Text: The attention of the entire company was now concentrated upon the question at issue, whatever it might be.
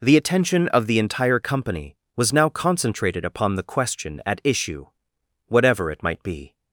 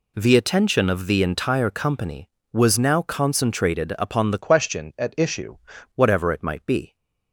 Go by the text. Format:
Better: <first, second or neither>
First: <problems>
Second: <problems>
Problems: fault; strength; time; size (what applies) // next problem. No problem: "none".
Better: first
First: none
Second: changes voice from "question" to "issue"; from 4.4 to 5.5 s; 1.1 s long